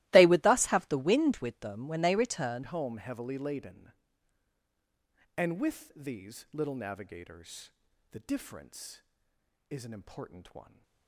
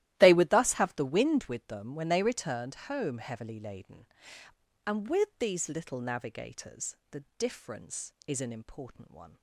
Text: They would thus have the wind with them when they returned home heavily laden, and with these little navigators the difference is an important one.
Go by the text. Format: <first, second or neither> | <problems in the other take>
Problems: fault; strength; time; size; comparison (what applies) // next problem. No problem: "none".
second | starts louder than the rest; strong; until 1.1 s; 17.5 dB; strong in the second // changes voice at "home"; from 2.6 s on; 8.2 s long // pauses between "navigators" and "the"; at 7.7 s; 0.40 s long; slight in the second